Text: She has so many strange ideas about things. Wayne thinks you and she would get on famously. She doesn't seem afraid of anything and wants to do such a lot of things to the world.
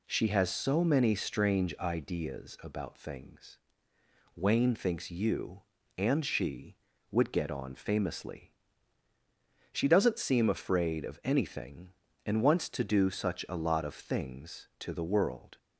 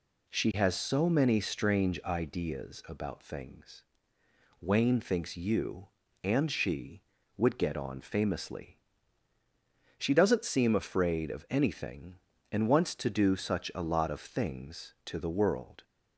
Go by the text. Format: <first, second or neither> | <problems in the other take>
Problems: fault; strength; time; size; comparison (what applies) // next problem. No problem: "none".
neither | none